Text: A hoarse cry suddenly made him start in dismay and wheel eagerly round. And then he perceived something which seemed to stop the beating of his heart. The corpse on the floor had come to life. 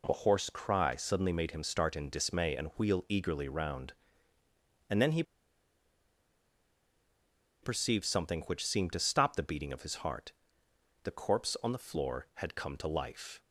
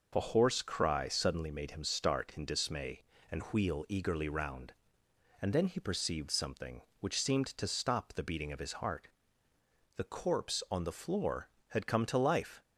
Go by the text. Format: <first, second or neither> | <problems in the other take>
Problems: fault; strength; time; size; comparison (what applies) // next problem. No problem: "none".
second | pauses between "he" and "perceived"; strong; at 5.2 s; 2.3 s long